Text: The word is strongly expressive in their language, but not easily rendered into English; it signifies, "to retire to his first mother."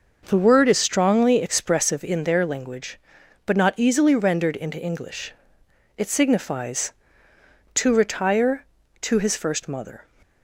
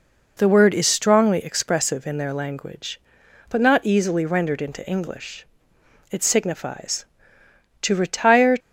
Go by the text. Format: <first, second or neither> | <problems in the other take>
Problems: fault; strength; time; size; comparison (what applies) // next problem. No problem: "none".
first | stops before "to his first mother"; at 8.5 s